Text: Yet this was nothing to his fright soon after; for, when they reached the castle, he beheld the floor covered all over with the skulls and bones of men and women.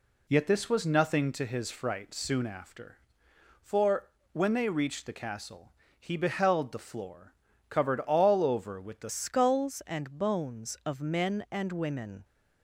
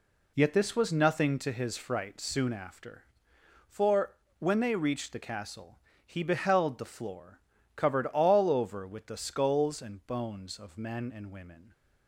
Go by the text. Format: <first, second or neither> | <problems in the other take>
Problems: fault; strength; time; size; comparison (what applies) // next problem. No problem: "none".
second | pauses between "floor" and "covered"; at 7.3 s; 0.38 s long; also in the second // changes voice at "skulls"; from 9.1 s on; 3.1 s long